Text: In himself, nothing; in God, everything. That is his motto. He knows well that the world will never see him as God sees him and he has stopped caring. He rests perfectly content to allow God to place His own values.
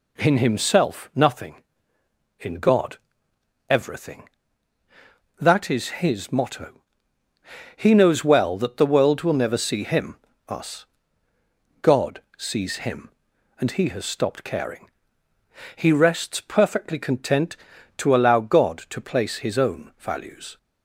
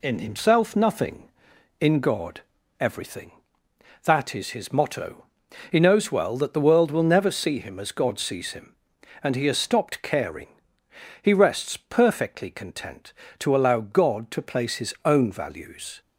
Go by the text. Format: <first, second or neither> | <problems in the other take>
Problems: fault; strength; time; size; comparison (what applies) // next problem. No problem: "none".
second | says "us" for "as"; at 10.4 s // pauses between "God" and "sees"; slight; at 12.2 s; 0.16 s long